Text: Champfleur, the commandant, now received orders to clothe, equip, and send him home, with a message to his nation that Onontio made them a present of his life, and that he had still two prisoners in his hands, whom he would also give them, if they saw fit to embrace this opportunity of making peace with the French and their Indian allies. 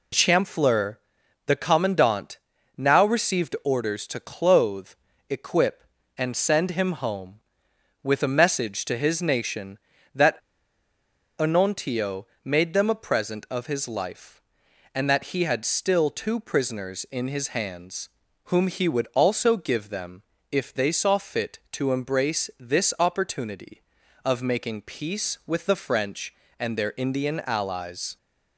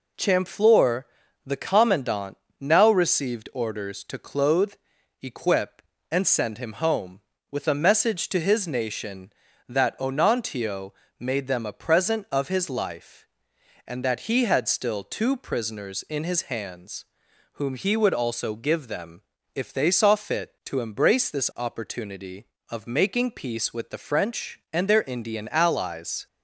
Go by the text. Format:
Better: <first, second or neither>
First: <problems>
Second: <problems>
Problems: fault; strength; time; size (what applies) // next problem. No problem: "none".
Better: second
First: pauses between "that" and "Onontio"; at 10.3 s; 0.99 s long // pauses between "Onontio" and "made"; slight; at 12.2 s; 0.20 s long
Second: pauses between "Onontio" and "made"; slight; at 10.9 s; 0.26 s long